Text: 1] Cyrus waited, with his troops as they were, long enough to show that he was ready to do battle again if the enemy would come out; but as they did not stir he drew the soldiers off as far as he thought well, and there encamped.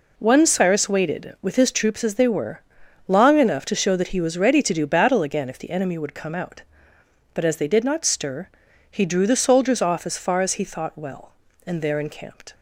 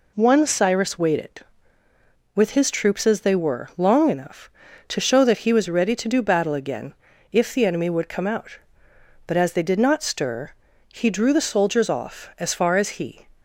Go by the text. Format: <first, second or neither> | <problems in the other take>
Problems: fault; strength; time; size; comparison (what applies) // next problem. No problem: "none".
first | pauses between "again" and "if"; at 6.9 s; 0.38 s long // pauses between "stir" and "he"; at 10.5 s; 0.38 s long; also in the first // stops before "thought well and there encamped"; at 13.3 s